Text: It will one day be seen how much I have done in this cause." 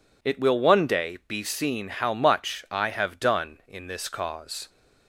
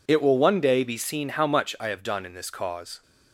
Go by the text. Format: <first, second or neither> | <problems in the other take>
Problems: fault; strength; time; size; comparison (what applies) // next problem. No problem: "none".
neither | none